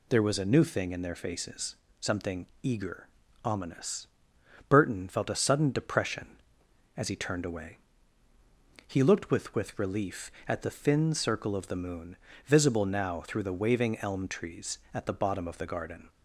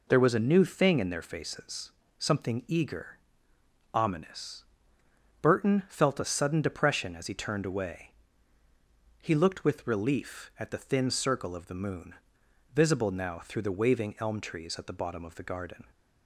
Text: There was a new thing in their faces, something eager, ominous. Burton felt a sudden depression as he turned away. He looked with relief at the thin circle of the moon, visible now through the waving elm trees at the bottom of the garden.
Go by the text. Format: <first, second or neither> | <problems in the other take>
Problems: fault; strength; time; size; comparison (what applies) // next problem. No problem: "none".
second | pauses between "something" and "eager"; slight; at 2.4 s; 0.16 s long // says "with" twice; at 9.5 s